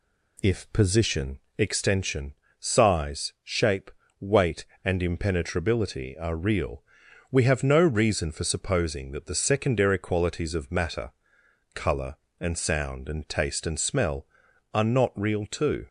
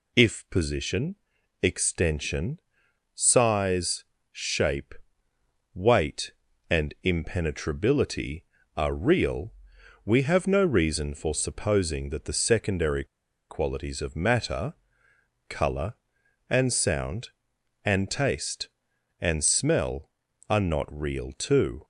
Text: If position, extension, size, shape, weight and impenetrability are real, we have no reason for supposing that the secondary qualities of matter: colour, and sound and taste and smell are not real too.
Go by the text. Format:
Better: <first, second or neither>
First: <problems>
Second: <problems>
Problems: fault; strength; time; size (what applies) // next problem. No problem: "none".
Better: first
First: none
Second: pauses between "secondary" and "qualities"; at 13.0 s; 0.45 s long